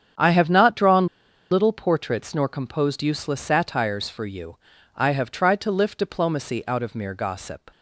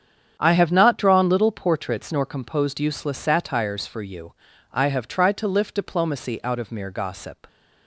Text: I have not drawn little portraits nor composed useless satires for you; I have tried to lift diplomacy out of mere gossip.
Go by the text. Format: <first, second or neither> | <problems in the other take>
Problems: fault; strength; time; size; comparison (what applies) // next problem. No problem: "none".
second | starts louder than the rest; strong; until 1.6 s; 8.5 dB; strong in the second // pauses between "drawn" and "little"; at 1.0 s; 0.43 s long